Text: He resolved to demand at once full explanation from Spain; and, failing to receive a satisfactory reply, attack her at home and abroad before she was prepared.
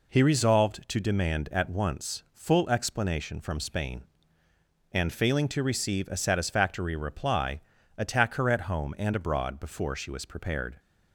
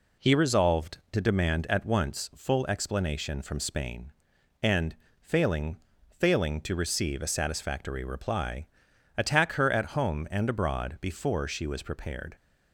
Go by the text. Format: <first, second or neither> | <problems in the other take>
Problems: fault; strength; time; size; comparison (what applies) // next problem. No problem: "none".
first | says "failing" twice; at 6.1 s